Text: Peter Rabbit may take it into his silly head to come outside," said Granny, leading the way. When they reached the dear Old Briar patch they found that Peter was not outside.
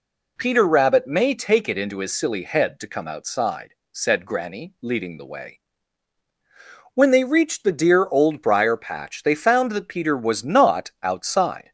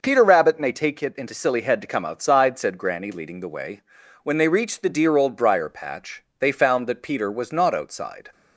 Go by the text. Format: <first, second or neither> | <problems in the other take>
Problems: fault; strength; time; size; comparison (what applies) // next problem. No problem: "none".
first | skips "his"; at 1.3 s // pauses between "patch" and "they"; slight; at 6.2 s; 0.16 s long